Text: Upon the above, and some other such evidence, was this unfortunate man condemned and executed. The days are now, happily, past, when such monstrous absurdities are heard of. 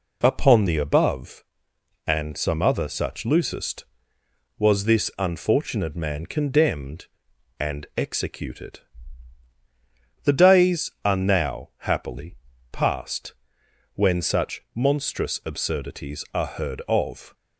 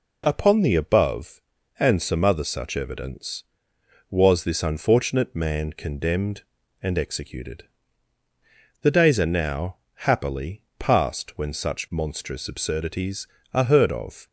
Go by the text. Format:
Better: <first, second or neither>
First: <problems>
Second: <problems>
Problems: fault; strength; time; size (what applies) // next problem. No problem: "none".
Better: second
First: says "loosest" for "evidence"; at 3.2 s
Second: none